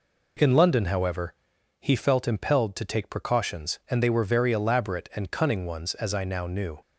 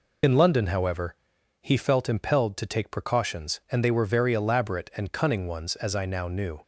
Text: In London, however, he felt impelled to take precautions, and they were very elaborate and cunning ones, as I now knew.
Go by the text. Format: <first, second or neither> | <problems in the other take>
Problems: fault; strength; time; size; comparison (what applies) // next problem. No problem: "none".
first | loses the start of "In"; at 0.2 s; 55 ms